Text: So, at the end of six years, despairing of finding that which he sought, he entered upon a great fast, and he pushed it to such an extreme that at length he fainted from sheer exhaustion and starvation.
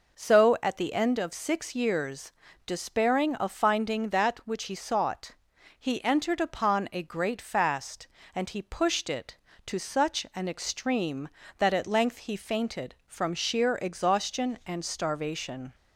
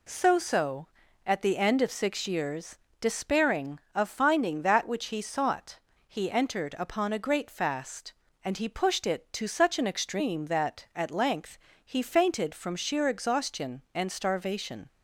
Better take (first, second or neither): first